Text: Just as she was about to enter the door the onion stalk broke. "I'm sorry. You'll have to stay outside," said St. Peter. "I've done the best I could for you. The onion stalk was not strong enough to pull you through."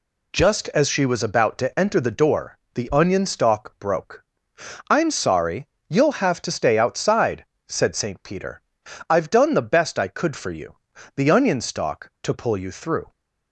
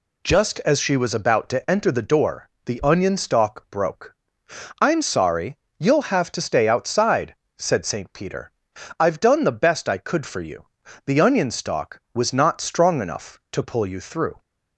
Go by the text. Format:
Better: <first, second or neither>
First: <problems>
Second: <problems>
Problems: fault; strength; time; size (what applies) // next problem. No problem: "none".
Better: second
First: pauses between "door" and "the"; slight; at 2.5 s; 0.16 s long // skips "was not strong enough"; at 12.1 s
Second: pauses between "door" and "the"; slight; at 2.4 s; 0.16 s long